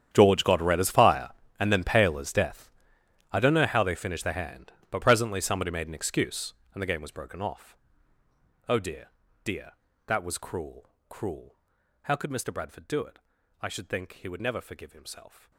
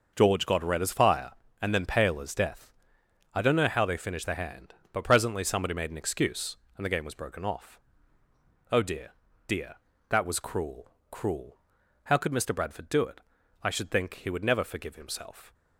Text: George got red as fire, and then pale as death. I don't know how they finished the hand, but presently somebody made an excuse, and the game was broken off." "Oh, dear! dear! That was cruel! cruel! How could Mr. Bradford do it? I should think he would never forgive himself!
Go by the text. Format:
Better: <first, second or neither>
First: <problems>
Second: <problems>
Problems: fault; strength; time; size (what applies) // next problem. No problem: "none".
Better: second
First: gets quieter; strong; throughout; 19.5 dB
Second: none